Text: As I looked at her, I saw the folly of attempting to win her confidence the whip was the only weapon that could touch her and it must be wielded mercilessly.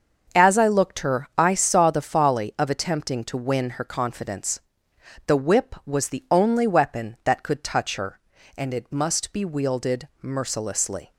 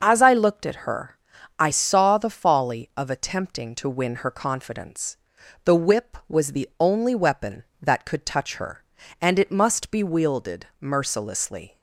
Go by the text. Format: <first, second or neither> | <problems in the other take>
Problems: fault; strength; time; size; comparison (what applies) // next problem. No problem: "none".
second | starts louder than the rest; until 1.4 s; 6.5 dB; noticeable in the second // skips "at"; at 1.0 s // pauses between "confidence" and "the"; noticeable; at 4.6 s; 0.64 s long; noticeable in the second